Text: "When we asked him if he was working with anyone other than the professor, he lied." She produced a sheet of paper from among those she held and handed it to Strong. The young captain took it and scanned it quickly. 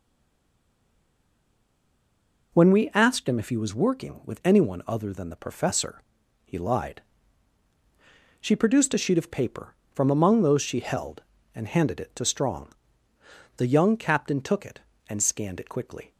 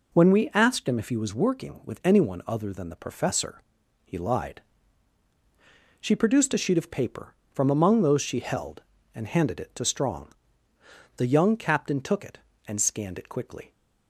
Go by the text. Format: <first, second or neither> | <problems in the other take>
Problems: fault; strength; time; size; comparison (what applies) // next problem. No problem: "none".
second | stays silent before the first word; strong; until 2.5 s; 2.5 s long